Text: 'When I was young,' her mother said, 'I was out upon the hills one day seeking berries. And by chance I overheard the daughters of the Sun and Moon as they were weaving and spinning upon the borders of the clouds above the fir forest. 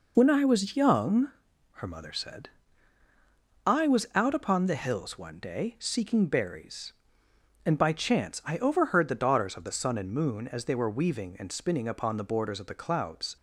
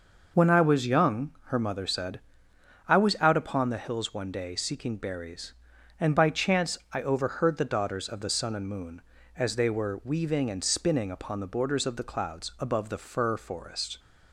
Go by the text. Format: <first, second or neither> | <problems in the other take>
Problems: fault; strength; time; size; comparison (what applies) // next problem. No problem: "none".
second | stops before "above the fir forest"; at 13.3 s